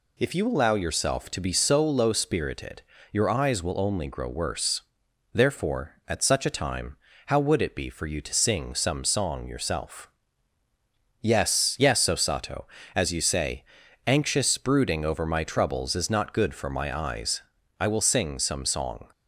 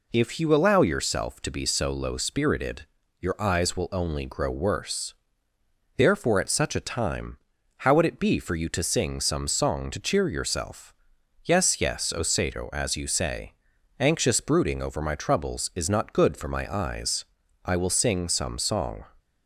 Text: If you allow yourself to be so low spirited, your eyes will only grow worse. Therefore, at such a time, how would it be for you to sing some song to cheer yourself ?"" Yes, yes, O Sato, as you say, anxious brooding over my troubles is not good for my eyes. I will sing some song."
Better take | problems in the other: second | skips "to cheer"; at 9.4 s

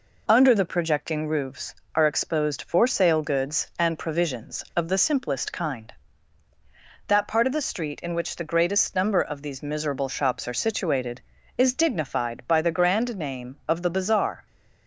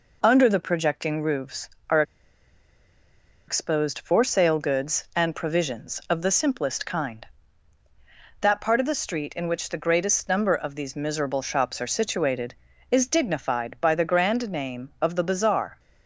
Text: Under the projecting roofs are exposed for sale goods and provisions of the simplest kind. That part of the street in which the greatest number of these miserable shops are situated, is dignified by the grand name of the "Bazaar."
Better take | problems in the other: first | pauses between "are" and "exposed"; strong; at 2.0 s; 1.4 s long

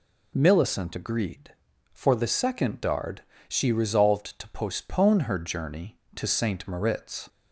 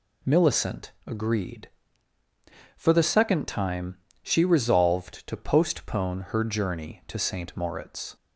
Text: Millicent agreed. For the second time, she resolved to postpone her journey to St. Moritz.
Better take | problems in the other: second | says "dard" for "time"; at 2.8 s

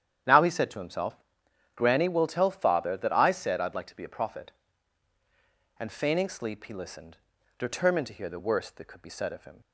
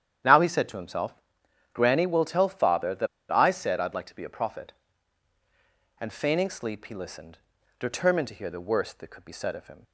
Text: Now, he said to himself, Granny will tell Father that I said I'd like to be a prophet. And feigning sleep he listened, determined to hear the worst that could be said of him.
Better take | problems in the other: first | starts louder than the rest; strong; until 1.8 s; 9.5 dB; strong in the first // pauses between "that" and "I"; slight; at 3.0 s; 0.23 s long

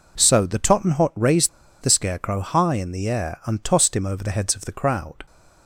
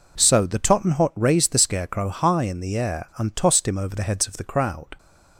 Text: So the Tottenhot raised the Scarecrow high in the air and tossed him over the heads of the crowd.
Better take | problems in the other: second | pauses between "raised" and "the"; slight; at 1.4 s; 0.34 s long

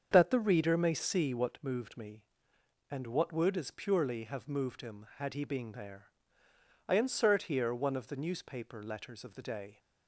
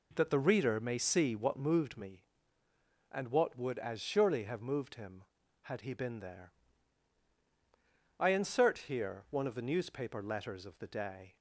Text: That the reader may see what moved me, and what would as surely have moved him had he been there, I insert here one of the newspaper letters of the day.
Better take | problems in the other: second | starts louder than the rest; strong; until 1.1 s; 7 dB // says "purely" for "surely"; at 3.7 s

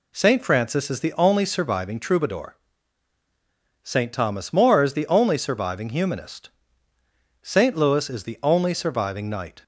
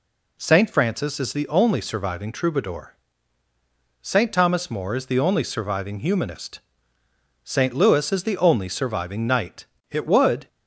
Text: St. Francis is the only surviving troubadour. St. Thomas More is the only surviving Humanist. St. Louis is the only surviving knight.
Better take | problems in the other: first | goes on to say "It would"; from 9.8 s on; 0.58 s long

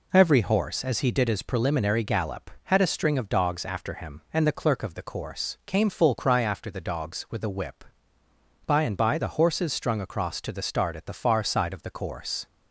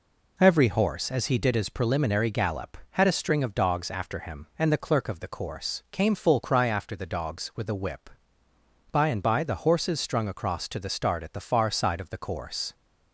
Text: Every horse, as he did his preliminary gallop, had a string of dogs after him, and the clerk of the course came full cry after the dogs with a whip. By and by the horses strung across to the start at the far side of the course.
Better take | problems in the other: neither | none

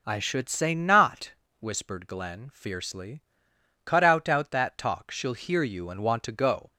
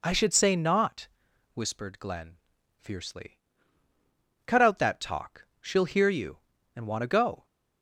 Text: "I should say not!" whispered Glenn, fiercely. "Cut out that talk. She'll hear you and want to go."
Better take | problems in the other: second | says "out" twice; at 4.2 s

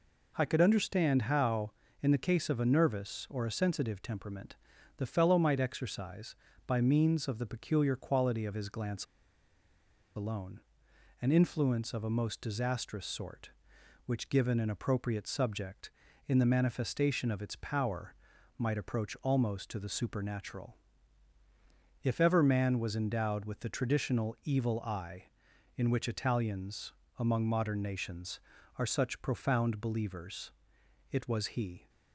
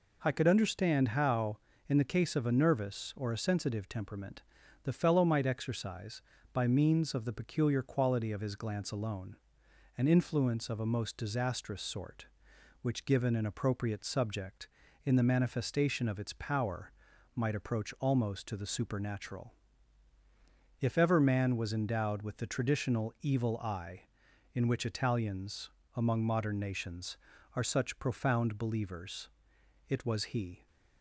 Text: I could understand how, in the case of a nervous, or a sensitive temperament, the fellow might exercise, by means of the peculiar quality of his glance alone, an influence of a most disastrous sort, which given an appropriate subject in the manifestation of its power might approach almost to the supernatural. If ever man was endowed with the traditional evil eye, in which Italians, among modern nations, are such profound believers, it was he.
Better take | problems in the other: second | pauses between "glance" and "alone"; at 9.0 s; 1.1 s long // pauses between "power" and "might"; at 18.1 s; 0.42 s long; also in the second

